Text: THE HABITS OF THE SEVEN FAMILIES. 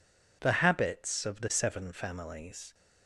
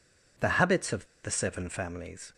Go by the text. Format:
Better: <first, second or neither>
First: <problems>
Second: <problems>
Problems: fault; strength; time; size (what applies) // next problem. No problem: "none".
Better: first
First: none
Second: pauses between "OF" and "THE"; slight; at 1.0 s; 0.16 s long